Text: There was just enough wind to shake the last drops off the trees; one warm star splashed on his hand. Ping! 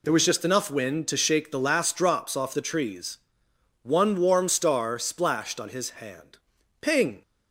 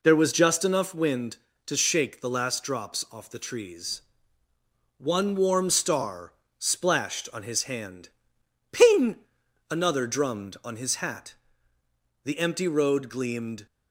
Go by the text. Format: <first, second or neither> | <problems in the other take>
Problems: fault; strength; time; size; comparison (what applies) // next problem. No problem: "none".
first | pauses between "star" and "splashed"; slight; at 6.3 s; 0.26 s long // goes on to say "another drummed on his hat The empty road gleamed"; strong; from 9.7 s on; 3.9 s long